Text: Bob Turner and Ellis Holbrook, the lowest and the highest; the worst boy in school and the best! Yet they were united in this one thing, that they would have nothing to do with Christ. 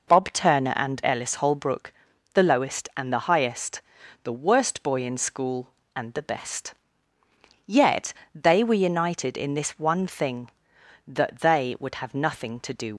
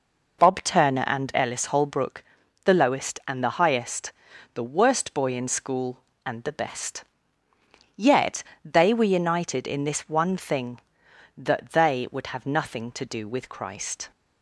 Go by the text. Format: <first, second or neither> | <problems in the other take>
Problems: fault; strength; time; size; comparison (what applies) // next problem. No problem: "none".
second | pauses between "Yet" and "they"; slight; at 8.1 s; 0.18 s long; slight in the second // stops before "with Christ"; at 12.9 s